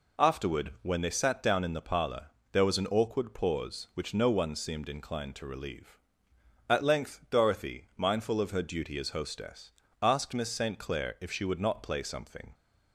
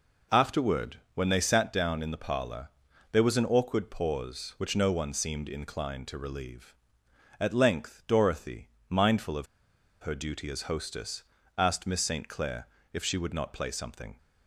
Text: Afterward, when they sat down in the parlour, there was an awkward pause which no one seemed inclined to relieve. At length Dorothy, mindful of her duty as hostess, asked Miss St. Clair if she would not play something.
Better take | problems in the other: first | pauses between "of" and "her"; noticeable; at 9.4 s; 0.55 s long // pauses between "Clair" and "if"; slight; at 12.6 s; 0.24 s long

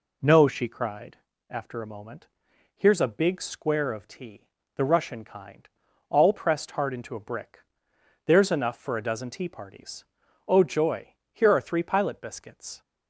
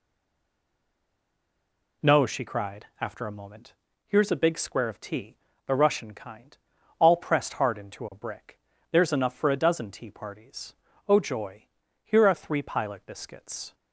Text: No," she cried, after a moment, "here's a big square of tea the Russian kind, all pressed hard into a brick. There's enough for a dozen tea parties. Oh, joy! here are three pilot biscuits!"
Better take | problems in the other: first | stays silent before the first word; noticeable; until 2.0 s; 2.0 s long // pauses between "tea" and "the"; slight; at 5.3 s; 0.30 s long; slight in the first

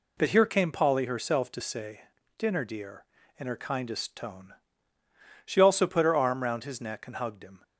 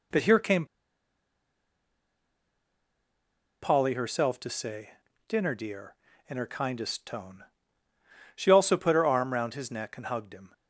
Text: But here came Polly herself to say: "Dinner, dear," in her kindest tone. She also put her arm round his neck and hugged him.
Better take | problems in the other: first | pauses between "came" and "Polly"; strong; at 0.6 s; 2.9 s long

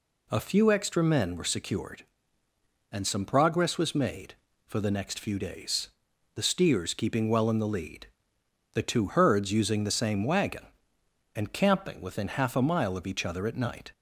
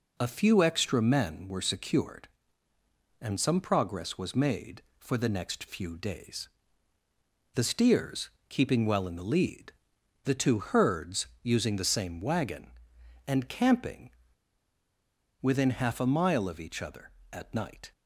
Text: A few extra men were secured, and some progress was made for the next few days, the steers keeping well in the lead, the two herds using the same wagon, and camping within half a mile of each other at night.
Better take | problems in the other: first | pauses between "steers" and "keeping"; slight; at 8.3 s; 0.18 s long // pauses between "herds" and "using"; slight; at 11.2 s; 0.16 s long // pauses between "camping" and "within"; strong; at 14.0 s; 1.3 s long

